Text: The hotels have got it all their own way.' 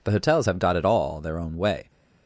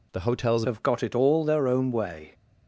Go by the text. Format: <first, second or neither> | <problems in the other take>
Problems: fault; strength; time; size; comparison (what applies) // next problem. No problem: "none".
first | changes voice at "have"; from 0.6 s on; 1.7 s long